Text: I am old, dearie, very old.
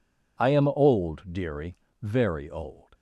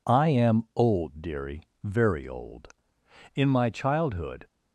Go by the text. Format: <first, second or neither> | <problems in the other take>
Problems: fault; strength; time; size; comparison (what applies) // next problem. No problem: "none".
first | goes on to say "In my childhood"; noticeable; from 3.3 s on; 1.1 s long